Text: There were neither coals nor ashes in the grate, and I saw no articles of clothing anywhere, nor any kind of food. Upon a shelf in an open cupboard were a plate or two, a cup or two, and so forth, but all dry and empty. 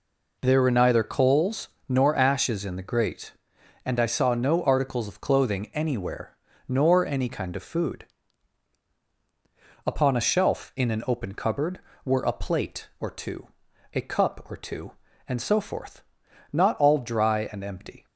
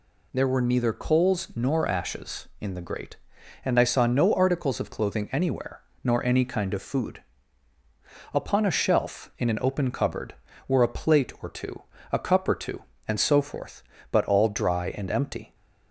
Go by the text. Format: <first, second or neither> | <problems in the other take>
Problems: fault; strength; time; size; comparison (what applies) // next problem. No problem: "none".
second | pauses between "coals" and "nor"; slight; at 1.6 s; 0.20 s long // says "not" for "but"; at 16.5 s